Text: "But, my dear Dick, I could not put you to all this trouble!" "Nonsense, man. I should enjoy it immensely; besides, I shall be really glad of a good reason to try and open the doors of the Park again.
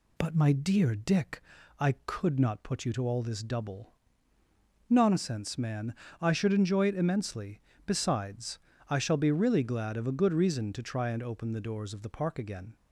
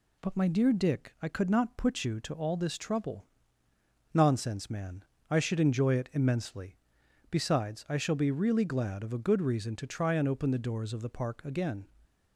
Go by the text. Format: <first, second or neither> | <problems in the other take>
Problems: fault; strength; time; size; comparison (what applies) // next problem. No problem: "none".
second | says "double" for "trouble"; at 3.4 s